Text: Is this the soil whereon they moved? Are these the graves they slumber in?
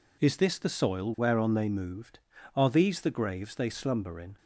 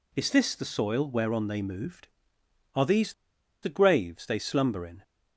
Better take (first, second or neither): first